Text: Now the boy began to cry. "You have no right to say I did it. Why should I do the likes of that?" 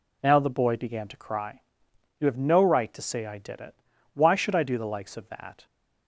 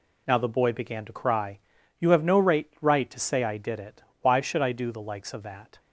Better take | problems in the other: first | says "right" twice; at 2.8 s

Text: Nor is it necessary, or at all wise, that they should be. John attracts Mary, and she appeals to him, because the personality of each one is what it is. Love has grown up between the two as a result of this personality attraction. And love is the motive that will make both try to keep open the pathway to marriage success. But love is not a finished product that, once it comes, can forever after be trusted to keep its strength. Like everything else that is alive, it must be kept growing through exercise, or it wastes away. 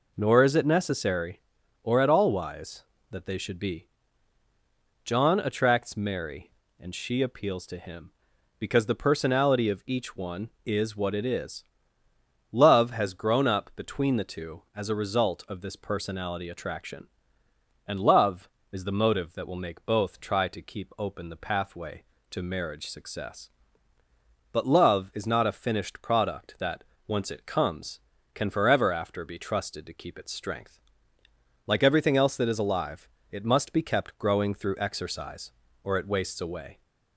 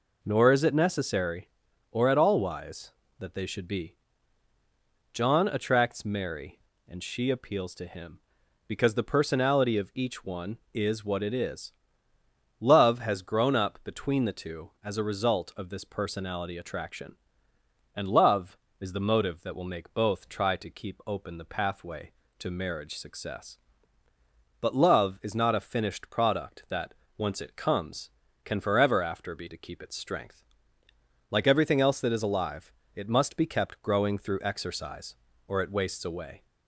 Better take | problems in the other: first | skips "trusted"; at 29.4 s

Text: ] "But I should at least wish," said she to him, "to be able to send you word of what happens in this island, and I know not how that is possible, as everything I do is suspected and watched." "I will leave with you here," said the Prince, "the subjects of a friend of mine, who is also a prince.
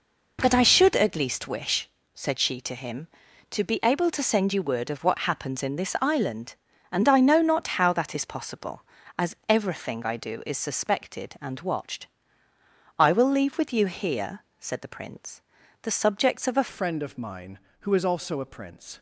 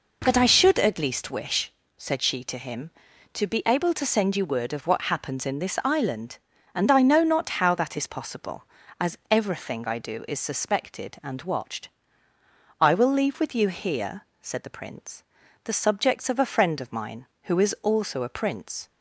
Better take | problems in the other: second | changes voice at "friend"; from 16.6 s on; 2.3 s long

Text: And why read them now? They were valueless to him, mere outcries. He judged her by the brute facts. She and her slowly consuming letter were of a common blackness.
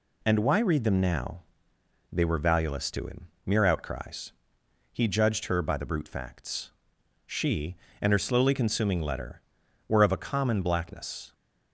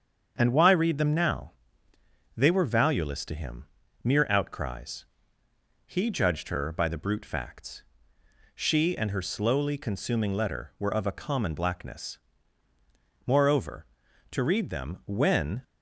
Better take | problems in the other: first | starts louder than the rest; strong; until 1.3 s; 7 dB // goes on to say "Moreover to read them when"; strong; from 13.2 s on; 2.3 s long

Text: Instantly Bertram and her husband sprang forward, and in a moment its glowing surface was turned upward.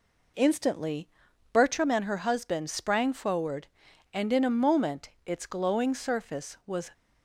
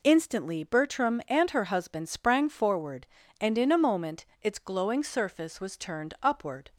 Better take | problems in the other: second | pauses between "Instantly" and "Bertram"; noticeable; at 1.0 s; 0.46 s long // pauses between "moment" and "its"; slight; at 5.0 s; 0.16 s long; slight in the second // stops before "turned upward"; at 6.9 s

